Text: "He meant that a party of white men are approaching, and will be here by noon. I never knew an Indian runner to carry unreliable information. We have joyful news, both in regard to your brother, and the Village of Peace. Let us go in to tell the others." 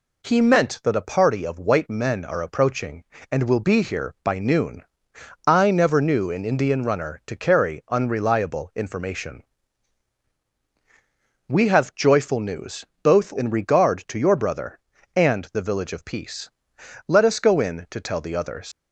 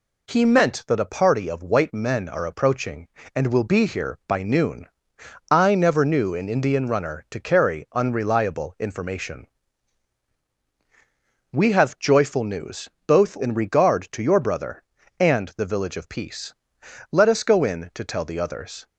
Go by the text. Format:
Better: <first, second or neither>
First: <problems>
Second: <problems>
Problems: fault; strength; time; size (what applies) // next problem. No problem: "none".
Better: second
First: leaves "others" unfinished; at 18.7 s; 125 ms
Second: none